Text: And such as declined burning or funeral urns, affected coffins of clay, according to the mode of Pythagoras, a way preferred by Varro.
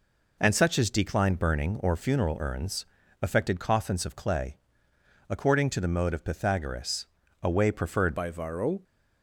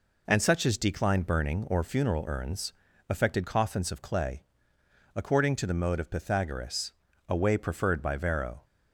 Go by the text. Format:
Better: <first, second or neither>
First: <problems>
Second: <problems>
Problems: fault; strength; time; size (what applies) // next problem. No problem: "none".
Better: second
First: changes voice at "by"; from 8.1 s on; 0.7 s long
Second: none